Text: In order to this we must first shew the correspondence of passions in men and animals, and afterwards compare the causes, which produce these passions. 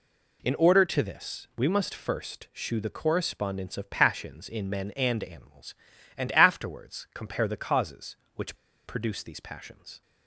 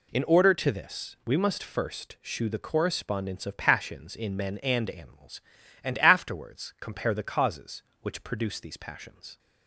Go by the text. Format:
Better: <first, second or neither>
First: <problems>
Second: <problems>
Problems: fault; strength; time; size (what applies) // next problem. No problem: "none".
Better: second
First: pauses between "which" and "produce"; slight; at 8.5 s; 0.30 s long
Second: none